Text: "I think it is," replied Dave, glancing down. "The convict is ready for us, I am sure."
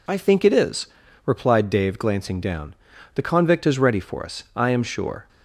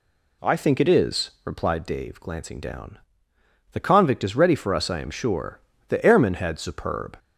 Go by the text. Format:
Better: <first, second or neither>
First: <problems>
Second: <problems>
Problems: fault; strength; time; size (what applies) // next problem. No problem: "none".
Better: first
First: none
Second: goes on to say "The airman had superb"; noticeable; from 5.8 s on; 1.3 s long